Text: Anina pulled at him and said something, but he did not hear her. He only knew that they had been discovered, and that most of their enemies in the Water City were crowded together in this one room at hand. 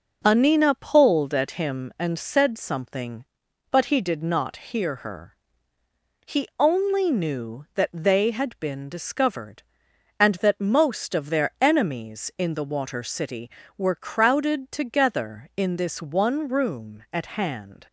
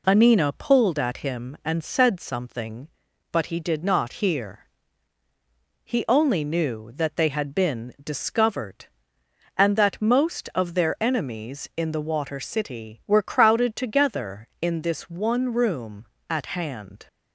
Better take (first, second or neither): first